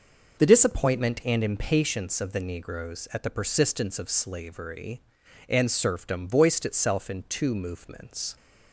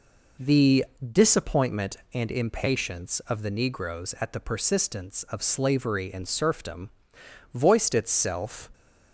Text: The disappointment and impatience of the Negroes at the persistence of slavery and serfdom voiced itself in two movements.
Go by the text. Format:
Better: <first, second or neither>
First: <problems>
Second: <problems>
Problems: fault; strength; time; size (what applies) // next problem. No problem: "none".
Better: first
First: none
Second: pauses between "The" and "disappointment"; slight; at 0.8 s; 0.26 s long // pauses between "serfdom" and "voiced"; noticeable; at 6.8 s; 0.64 s long // stops before "in two movements"; at 8.7 s